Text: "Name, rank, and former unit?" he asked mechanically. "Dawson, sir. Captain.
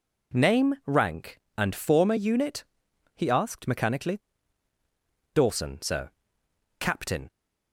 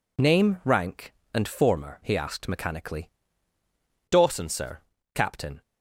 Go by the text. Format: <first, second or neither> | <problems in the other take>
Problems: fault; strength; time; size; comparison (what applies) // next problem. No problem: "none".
first | skips "unit"; at 2.0 s